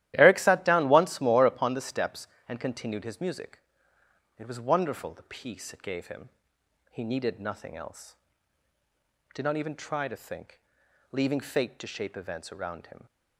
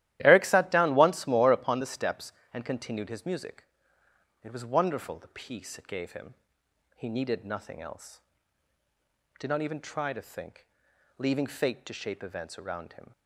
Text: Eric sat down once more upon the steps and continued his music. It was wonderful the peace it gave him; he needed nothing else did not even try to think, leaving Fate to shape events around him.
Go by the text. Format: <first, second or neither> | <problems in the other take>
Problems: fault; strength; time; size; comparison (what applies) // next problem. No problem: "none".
neither | starts louder than the rest; strong; the same in both